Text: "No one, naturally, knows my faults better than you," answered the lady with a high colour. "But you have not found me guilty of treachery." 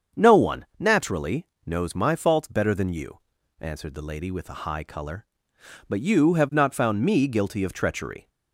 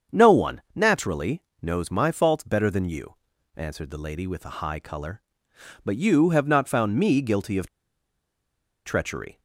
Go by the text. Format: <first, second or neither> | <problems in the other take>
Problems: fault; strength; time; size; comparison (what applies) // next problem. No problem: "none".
first | starts louder than the rest; strong; until 1.2 s; 7 dB; strong in the first // pauses between "of" and "treachery"; at 7.6 s; 1.1 s long